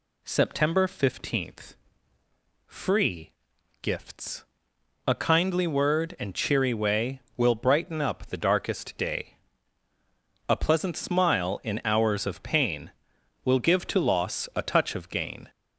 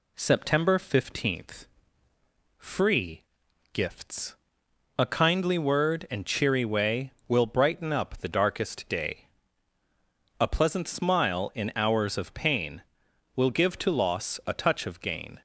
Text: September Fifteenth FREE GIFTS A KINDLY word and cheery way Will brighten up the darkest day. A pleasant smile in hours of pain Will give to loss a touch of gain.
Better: second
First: gets louder; noticeable; throughout; 5 dB // pauses between "Fifteenth" and "FREE"; noticeable; at 1.7 s; 0.90 s long // pauses between "FREE" and "GIFTS"; noticeable; at 3.3 s; 0.48 s long // pauses between "GIFTS" and "A"; noticeable; at 4.4 s; 0.60 s long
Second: pauses between "Fifteenth" and "FREE"; noticeable; at 1.6 s; 0.90 s long // pauses between "FREE" and "GIFTS"; noticeable; at 3.2 s; 0.48 s long // pauses between "GIFTS" and "A"; noticeable; at 4.3 s; 0.60 s long

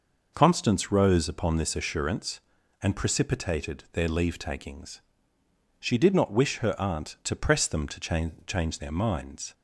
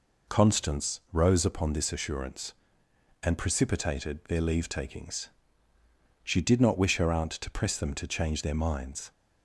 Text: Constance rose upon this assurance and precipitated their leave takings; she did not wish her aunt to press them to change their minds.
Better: second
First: says "change" twice; at 8.4 s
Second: none

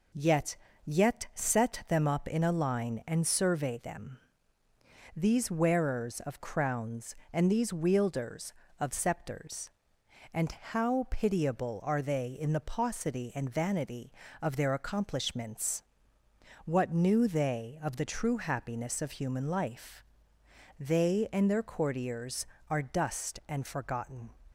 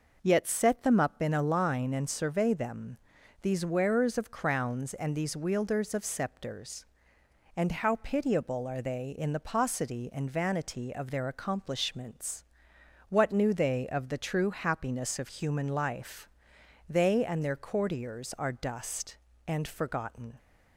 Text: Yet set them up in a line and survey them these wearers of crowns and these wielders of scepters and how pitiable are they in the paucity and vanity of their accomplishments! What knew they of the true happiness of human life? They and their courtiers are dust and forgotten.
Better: second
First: says "Yet" twice; at 0.8 s // pauses between "them" and "these"; noticeable; at 4.1 s; 0.98 s long // pauses between "and" and "how"; slight; at 10.5 s; 0.20 s long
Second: pauses between "them" and "these"; at 2.9 s; 0.44 s long

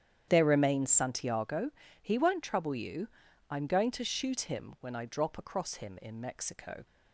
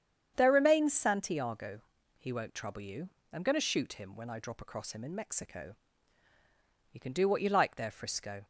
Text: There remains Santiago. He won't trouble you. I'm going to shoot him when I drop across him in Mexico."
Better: first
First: starts louder than the rest; strong; until 1.2 s; 9 dB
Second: starts louder than the rest; strong; until 1.3 s; 8.5 dB // goes on to say "You can do what you like there Frisco"; from 6.9 s on; 1.5 s long

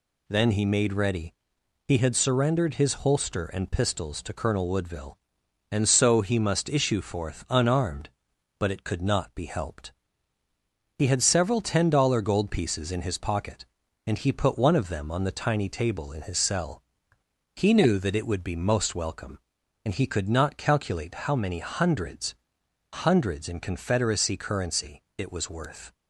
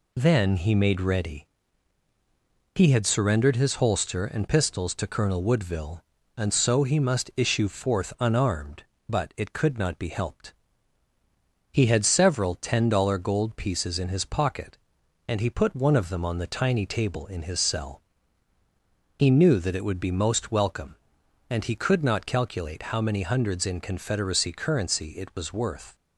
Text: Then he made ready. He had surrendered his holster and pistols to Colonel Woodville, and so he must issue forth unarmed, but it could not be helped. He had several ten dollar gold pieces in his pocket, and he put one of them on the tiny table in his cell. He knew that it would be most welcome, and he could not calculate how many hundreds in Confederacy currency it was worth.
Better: second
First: says "hundreds" twice; at 22.9 s // pauses between "currency" and "it"; slight; at 25.0 s; 0.16 s long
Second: none

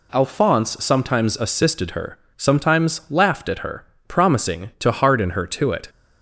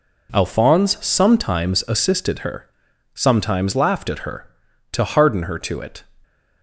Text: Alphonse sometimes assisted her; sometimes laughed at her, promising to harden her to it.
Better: first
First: none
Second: skips "promising"; at 4.6 s

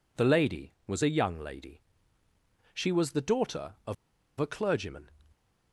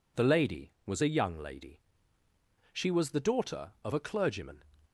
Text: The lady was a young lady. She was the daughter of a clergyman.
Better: second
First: pauses between "of" and "a"; at 3.9 s; 0.44 s long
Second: none

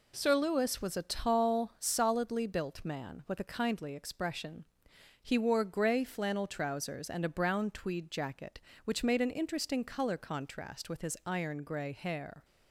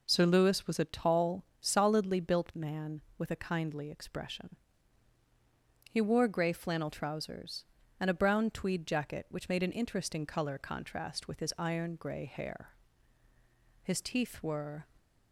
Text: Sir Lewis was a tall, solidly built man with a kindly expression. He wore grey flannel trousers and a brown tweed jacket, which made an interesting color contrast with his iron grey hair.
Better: first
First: none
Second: goes on to say "His teeth were"; noticeable; from 13.8 s on; 1.0 s long

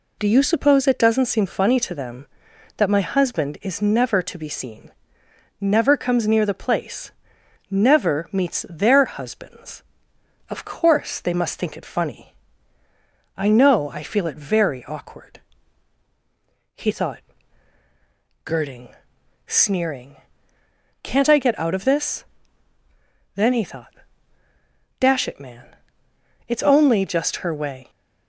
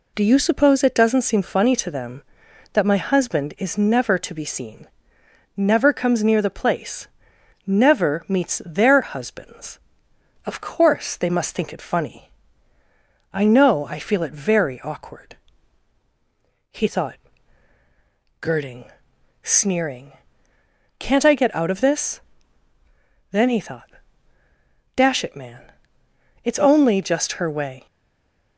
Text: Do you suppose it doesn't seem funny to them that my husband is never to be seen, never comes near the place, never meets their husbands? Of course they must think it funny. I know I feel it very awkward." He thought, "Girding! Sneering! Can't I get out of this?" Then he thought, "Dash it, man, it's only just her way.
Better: first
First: none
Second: stays silent after the last word; slight; from 27.8 s on; 0.7 s long

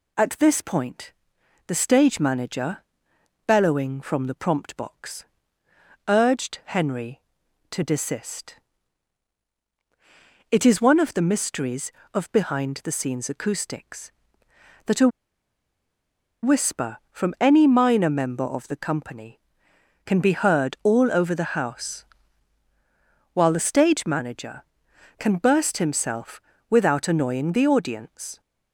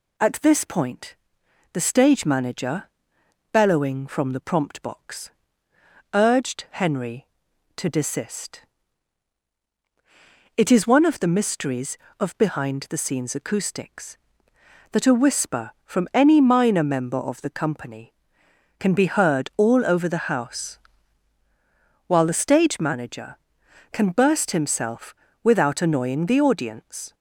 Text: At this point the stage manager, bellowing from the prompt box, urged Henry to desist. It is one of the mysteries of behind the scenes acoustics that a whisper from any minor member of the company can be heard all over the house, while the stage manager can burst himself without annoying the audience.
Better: second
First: pauses between "point" and "the"; noticeable; at 1.1 s; 0.54 s long // pauses between "a" and "whisper"; strong; at 15.0 s; 1.3 s long // pauses between "himself" and "without"; slight; at 26.3 s; 0.30 s long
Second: pauses between "point" and "the"; noticeable; at 1.1 s; 0.56 s long // pauses between "himself" and "without"; slight; at 25.1 s; 0.30 s long

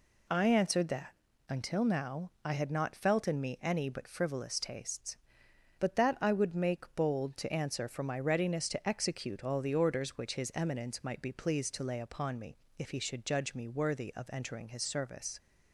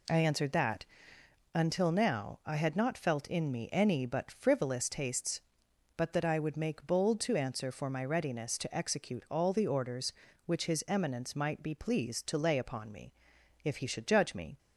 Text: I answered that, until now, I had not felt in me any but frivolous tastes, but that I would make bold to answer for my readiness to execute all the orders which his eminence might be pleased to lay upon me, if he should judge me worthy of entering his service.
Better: first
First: none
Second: stops before "worthy of entering his service"; at 14.5 s

